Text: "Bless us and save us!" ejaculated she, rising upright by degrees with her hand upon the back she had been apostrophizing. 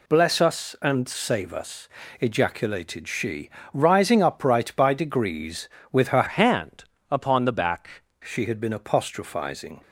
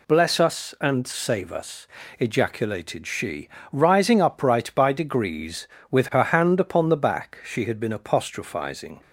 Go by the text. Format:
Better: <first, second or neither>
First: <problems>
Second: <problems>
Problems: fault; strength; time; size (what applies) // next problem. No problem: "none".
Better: second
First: changes voice from "hand" to "back"; from 6.2 to 8.0 s; 1.8 s long // pauses between "hand" and "upon"; slight; at 6.8 s; 0.26 s long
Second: none